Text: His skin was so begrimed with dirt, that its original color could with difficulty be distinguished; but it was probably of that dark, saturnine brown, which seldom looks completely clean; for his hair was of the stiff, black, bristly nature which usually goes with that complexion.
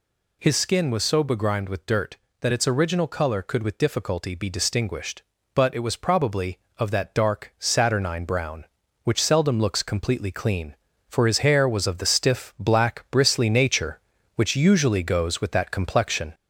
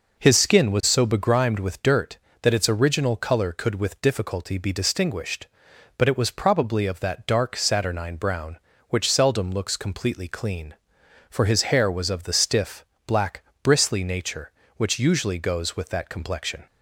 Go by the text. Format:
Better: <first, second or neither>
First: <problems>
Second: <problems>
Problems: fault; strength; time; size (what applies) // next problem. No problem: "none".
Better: second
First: gets louder; slight; throughout; 3 dB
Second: none